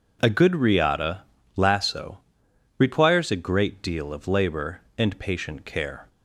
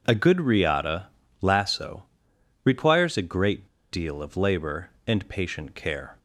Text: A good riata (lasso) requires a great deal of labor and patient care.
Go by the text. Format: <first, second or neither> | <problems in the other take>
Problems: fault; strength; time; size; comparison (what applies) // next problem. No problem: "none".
first | pauses between "great" and "deal"; slight; at 3.6 s; 0.24 s long